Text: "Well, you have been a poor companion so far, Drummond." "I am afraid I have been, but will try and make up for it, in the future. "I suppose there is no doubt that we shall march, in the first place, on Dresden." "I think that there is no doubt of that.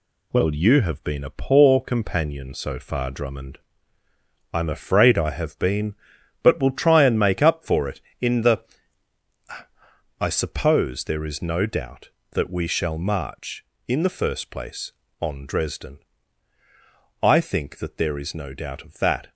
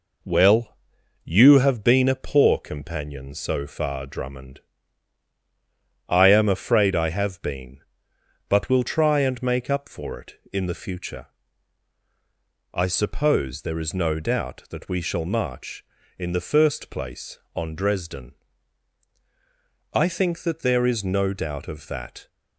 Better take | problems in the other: second | skips "future"; at 9.4 s

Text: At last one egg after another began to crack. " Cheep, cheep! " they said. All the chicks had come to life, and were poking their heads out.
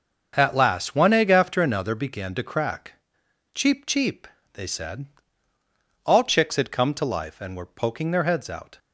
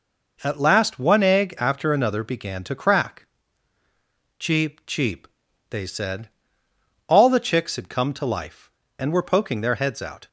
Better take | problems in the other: second | starts louder than the rest; until 1.3 s; 6.5 dB // skips "the"; at 6.2 s

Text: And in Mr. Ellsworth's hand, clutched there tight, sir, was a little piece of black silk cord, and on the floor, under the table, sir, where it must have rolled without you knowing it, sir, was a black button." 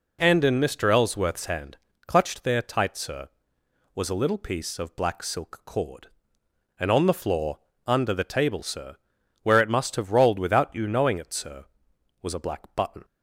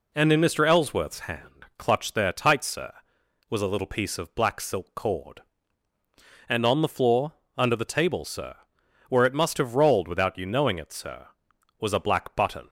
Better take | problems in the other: neither | none

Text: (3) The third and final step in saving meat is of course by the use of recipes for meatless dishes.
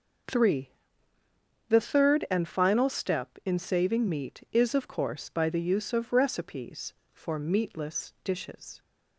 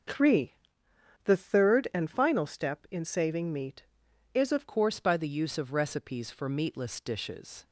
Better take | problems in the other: first | starts louder than the rest; until 1.7 s; 6.5 dB // changes voice at "course"; from 4.6 s on; 3.0 s long

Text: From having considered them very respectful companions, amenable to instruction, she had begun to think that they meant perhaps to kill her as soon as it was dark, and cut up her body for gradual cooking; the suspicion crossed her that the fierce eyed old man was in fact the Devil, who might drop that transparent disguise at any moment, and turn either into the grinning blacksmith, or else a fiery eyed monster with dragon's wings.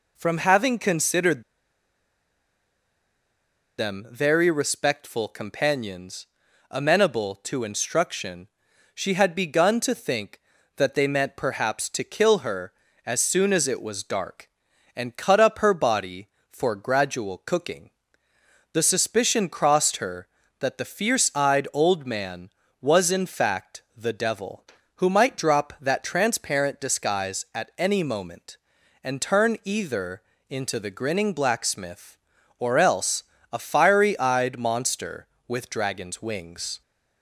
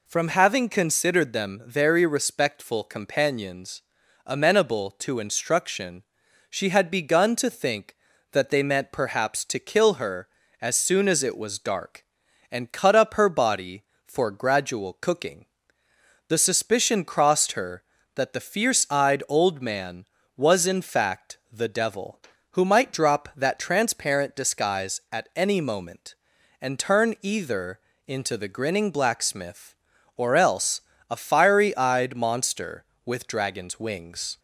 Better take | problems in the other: second | pauses between "considered" and "them"; strong; at 1.4 s; 2.3 s long // pauses between "either" and "into"; slight; at 30.2 s; 0.28 s long; slight in the second // pauses between "else" and "a"; slight; at 33.2 s; 0.28 s long; slight in the second

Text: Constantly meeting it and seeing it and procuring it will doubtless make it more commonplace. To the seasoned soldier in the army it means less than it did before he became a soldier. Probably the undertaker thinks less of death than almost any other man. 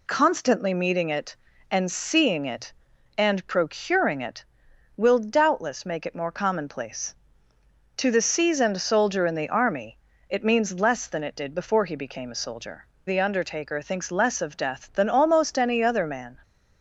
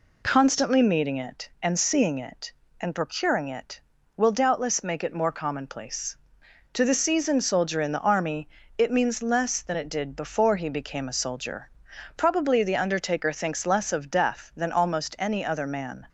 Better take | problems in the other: second | pauses between "army" and "it"; slight; at 9.9 s; 0.32 s long; slight in the second // skips "Probably"; at 12.9 s

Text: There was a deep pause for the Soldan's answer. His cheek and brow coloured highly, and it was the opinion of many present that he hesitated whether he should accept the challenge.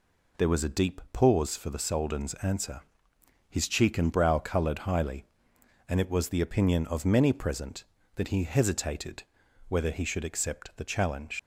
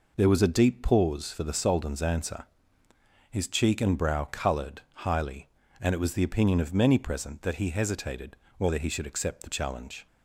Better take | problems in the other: second | pauses between "hesitated" and "whether"; noticeable; at 9.2 s; 0.46 s long; slight in the second // leaves "challenge" unfinished; at 11.3 s; 90 ms

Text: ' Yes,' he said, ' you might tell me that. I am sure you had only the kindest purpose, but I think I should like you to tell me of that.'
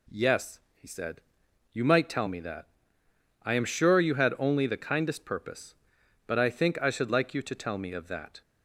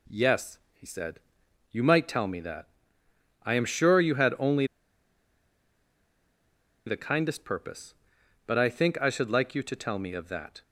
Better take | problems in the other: first | pauses between "only" and "the"; strong; at 4.6 s; 2.2 s long

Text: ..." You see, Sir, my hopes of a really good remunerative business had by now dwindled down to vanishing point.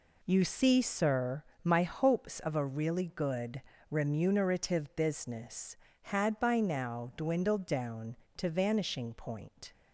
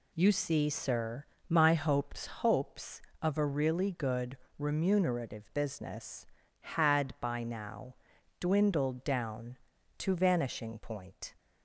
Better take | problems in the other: first | says "hopes" twice; at 2.2 s // pauses between "good" and "remunerative"; slight; at 4.3 s; 0.22 s long; slight in the first // pauses between "now" and "dwindled"; at 7.9 s; 0.44 s long

